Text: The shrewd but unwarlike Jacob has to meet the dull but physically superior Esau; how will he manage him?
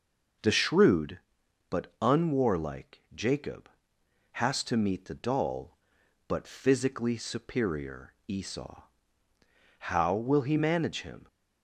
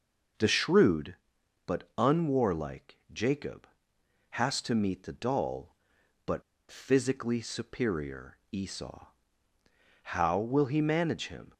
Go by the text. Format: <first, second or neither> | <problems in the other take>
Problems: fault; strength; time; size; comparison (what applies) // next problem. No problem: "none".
first | pauses between "unwarlike" and "Jacob"; slight; at 2.9 s; 0.16 s long // pauses between "but" and "physically"; slight; at 6.4 s; 0.28 s long